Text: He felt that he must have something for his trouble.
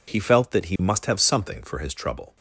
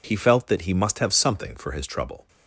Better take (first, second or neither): neither